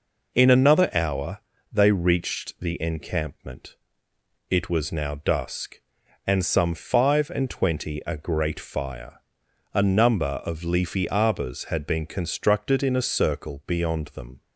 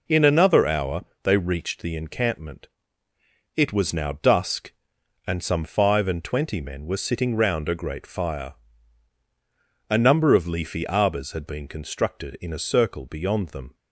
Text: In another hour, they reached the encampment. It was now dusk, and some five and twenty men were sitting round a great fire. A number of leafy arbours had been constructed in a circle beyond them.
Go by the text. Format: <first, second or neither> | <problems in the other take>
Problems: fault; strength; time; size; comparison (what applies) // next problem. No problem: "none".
second | skips "men were sitting round"; at 8.0 s